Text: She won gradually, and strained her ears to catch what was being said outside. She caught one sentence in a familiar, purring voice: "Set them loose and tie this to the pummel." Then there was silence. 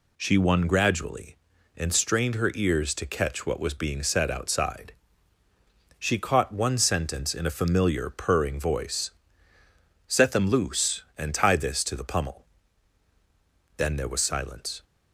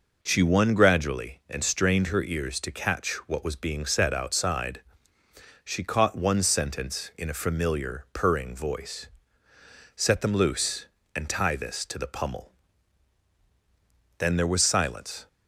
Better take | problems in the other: neither | none

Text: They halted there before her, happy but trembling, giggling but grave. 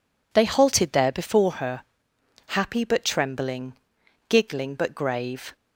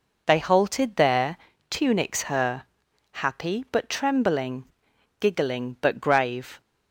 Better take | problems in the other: first | says "tunics" for "before"; at 1.6 s

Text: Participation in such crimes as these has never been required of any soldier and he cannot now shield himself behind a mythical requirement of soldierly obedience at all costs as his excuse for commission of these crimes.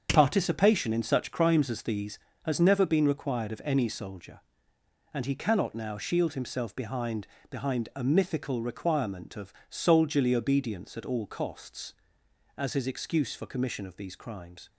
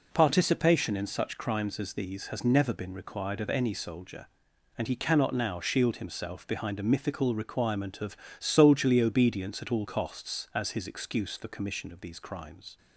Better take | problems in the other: second | starts louder than the rest; strong; until 1.1 s; 7 dB // says "behind" twice; at 7.5 s // pauses between "of" and "soldierly"; slight; at 9.5 s; 0.16 s long; slight in the second

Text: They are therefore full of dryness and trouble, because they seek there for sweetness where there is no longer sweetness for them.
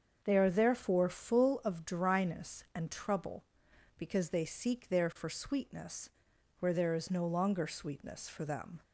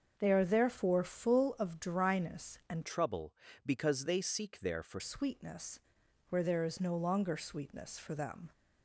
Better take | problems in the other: first | starts louder than the rest; until 1.1 s; 6.5 dB; also in the first // changes voice from "trouble" to "for"; from 2.8 to 4.9 s; 2.1 s long // pauses between "sweetness" and "where"; noticeable; at 5.8 s; 0.50 s long; noticeable in the first

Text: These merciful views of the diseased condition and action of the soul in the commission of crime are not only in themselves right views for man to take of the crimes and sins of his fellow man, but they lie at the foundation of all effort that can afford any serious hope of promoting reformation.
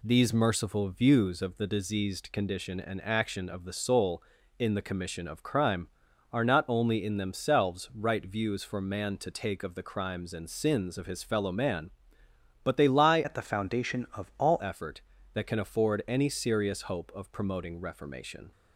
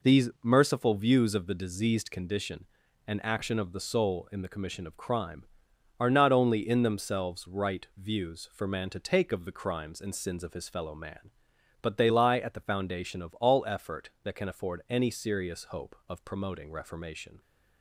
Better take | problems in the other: second | changes voice from "at" to "all"; from 13.2 to 14.6 s; 1.4 s long

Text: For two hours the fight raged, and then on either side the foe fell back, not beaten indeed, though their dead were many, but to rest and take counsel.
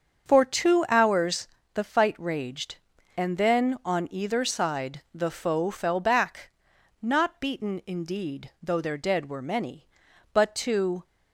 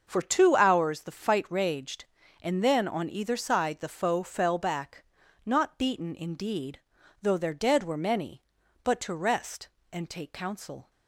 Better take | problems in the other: second | starts louder than the rest; until 1.3 s; 7 dB; also in the second // pauses between "hours" and "the"; slight; at 1.4 s; 0.28 s long // stops before "rest and take counsel"; at 11.0 s

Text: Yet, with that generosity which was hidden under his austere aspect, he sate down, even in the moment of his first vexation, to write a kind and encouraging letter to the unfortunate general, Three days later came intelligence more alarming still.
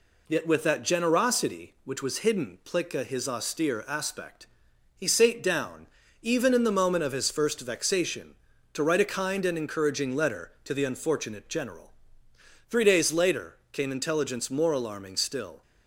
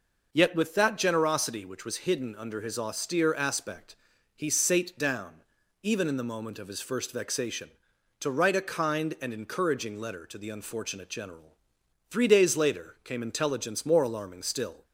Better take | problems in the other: second | says "plica" for "under"; at 2.6 s

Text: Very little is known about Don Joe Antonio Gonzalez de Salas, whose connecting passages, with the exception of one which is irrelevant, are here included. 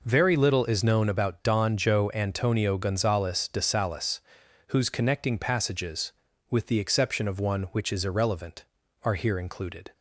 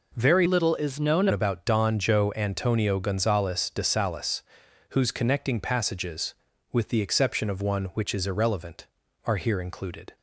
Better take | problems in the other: first | changes voice from "little" to "known"; from 0.4 to 1.2 s; 0.8 s long

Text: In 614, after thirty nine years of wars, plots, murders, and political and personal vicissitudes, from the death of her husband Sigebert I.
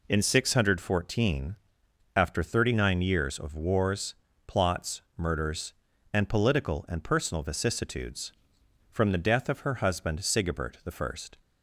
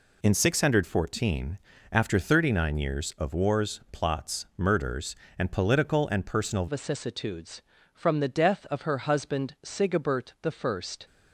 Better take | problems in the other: first | changes voice at "vicissitudes"; from 6.6 s on; 4.2 s long

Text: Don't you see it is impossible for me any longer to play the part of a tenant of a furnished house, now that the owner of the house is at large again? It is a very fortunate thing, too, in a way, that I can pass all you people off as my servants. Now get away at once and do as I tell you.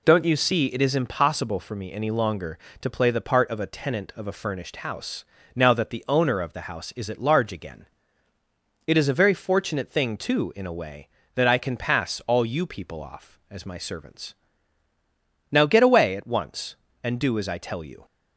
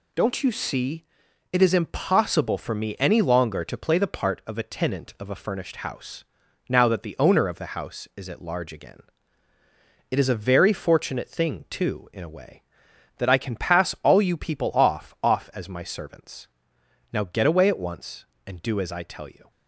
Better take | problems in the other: first | pauses between "see" and "it"; noticeable; at 1.0 s; 0.48 s long // says "off" twice; at 15.2 s

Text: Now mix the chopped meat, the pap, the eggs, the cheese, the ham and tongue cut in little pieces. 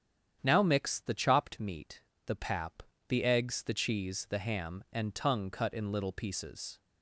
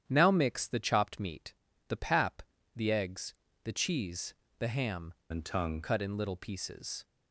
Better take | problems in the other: first | starts louder than the rest; strong; until 1.0 s; 9.5 dB; strong in the first // changes voice from "and" to "tongue"; from 5.3 to 5.8 s; 0.5 s long

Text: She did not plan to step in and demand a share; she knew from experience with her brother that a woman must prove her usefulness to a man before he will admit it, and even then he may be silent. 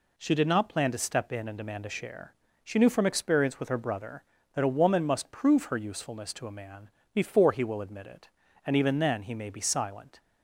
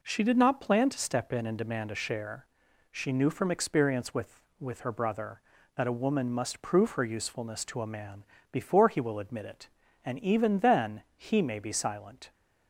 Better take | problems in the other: first | says "with" twice; at 4.5 s // pauses between "man" and "before"; slight; at 8.2 s; 0.26 s long; slight in the first

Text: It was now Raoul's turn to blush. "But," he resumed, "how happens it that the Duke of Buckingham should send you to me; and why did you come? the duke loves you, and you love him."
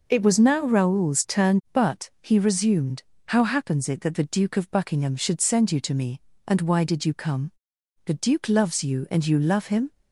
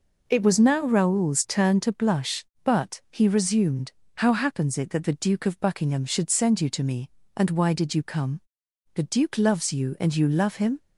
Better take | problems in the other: second | skips "to blush"; at 1.6 s

